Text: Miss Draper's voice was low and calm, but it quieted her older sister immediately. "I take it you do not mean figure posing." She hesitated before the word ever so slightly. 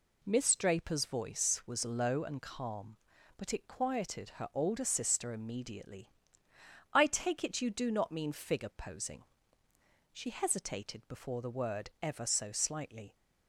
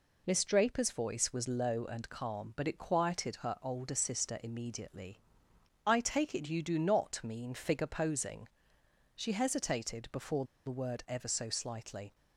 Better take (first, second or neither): first